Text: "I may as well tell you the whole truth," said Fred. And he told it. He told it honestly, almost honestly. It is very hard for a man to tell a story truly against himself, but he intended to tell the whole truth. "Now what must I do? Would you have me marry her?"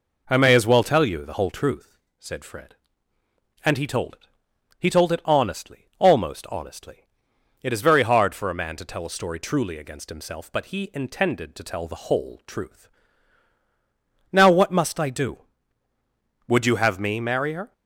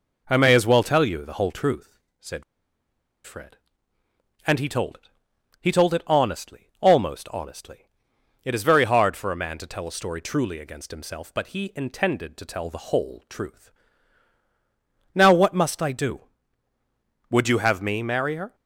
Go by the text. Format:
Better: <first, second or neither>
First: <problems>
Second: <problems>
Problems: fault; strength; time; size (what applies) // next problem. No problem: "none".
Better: first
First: none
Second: pauses between "said" and "Fred"; noticeable; at 2.4 s; 0.83 s long